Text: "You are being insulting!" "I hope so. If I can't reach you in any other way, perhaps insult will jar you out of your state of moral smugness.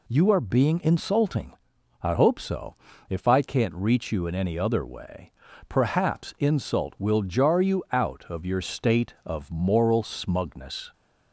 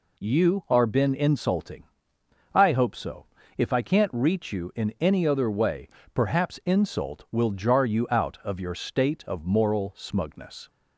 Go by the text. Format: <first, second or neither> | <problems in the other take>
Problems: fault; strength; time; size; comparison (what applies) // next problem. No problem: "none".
first | says "been" for "being"; at 0.8 s